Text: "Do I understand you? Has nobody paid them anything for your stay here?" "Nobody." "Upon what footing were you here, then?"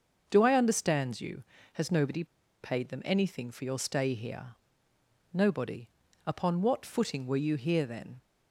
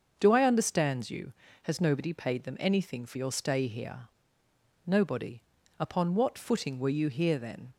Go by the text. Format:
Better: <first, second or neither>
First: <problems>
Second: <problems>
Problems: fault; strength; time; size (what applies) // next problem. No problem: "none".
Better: second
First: starts louder than the rest; until 1.2 s; 6.5 dB // pauses between "nobody" and "paid"; at 2.2 s; 0.37 s long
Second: starts louder than the rest; until 1.1 s; 6.5 dB